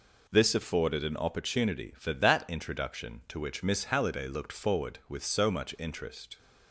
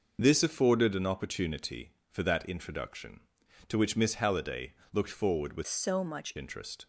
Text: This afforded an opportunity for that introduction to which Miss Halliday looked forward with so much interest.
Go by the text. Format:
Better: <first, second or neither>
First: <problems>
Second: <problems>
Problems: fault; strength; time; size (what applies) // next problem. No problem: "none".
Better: first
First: none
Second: pauses between "Halliday" and "looked"; slight; at 4.7 s; 0.18 s long // changes voice from "so" to "much"; from 5.6 to 6.3 s; 0.7 s long